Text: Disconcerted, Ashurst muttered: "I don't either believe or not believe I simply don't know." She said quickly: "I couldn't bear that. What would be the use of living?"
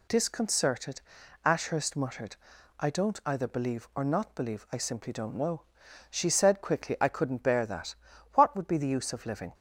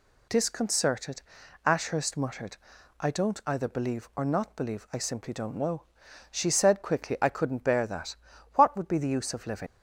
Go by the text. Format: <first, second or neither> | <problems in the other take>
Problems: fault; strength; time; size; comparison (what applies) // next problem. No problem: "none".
first | leaves "living" unfinished; at 9.6 s; 75 ms